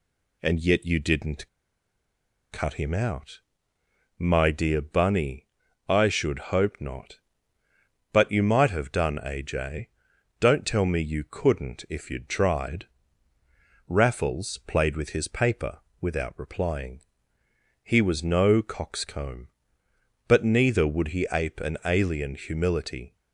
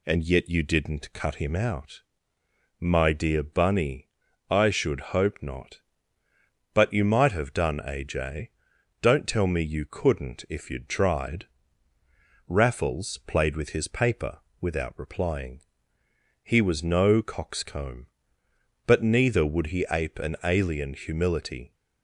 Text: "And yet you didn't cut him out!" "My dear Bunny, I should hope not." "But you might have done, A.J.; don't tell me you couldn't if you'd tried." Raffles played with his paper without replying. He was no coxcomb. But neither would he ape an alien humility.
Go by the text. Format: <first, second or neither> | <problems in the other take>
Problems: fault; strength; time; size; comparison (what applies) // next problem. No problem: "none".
second | pauses between "didn't" and "cut"; at 1.4 s; 1.0 s long // pauses between "paper" and "without"; slight; at 15.7 s; 0.22 s long; slight in the second